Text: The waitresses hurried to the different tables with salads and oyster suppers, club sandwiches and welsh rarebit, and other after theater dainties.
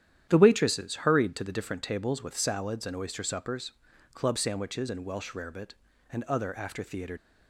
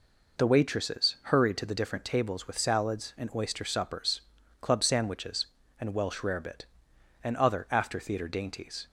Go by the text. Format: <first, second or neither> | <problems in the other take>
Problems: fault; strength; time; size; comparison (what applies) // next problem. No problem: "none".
second | starts louder than the rest; strong; until 1.3 s; 10.5 dB // stops before "dainties"; at 7.1 s